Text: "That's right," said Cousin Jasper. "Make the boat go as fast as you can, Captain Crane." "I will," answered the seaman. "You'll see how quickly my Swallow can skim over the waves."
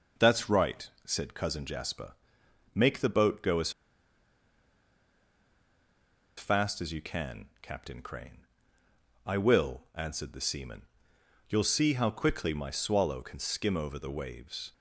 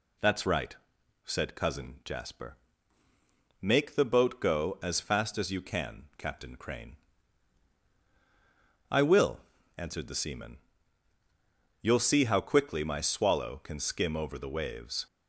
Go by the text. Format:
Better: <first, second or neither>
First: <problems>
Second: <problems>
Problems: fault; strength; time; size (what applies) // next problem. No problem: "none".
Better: second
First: pauses between "as" and "fast"; strong; at 3.6 s; 2.6 s long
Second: none